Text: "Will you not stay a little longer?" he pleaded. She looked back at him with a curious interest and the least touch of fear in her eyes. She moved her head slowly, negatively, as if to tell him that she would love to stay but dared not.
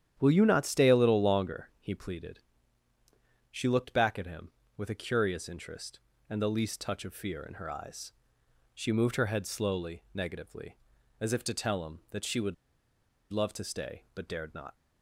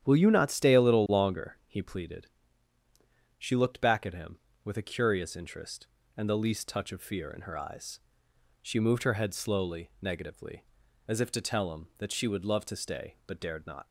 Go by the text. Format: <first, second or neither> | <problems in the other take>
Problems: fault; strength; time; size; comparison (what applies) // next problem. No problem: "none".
second | starts louder than the rest; strong; until 1.2 s; 10 dB; strong in the second // pauses between "would" and "love"; noticeable; at 12.5 s; 0.78 s long